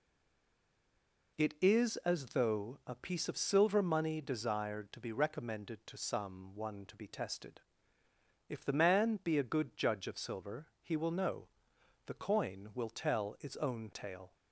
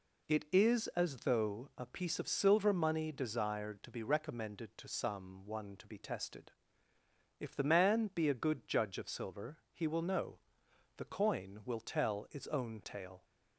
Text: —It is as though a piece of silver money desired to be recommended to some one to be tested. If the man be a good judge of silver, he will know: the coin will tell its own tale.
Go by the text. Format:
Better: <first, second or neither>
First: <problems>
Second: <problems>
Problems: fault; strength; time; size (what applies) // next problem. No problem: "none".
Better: second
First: stays silent before the first word; noticeable; until 1.3 s; 1.3 s long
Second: none